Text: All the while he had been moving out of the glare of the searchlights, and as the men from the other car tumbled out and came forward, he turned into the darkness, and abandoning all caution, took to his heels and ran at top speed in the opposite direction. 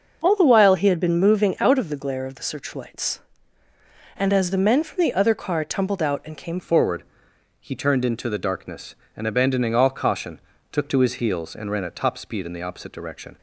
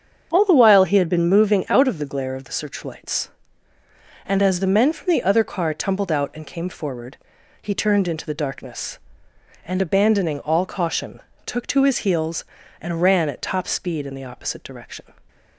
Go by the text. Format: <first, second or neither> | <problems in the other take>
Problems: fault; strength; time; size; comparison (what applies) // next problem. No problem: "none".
second | starts louder than the rest; noticeable; until 1.2 s; 6 dB; strong in the second // changes voice at "forward"; from 6.5 s on; 6.8 s long